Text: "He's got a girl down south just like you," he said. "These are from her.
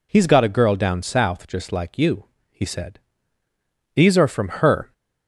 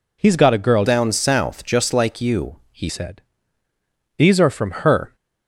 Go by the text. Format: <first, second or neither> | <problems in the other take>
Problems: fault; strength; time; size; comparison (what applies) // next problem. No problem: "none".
first | changes voice from "down" to "he"; from 0.8 to 2.8 s; 2.0 s long // pauses between "from" and "her"; slight; at 4.6 s; 0.16 s long; slight in the first